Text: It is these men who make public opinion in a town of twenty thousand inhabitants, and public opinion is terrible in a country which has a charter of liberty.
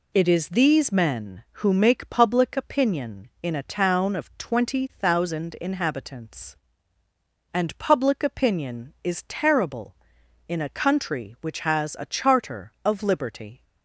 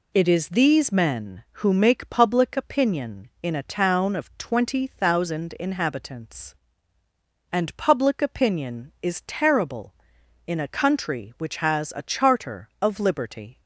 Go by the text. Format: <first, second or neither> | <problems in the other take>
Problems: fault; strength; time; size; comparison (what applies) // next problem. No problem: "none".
neither | none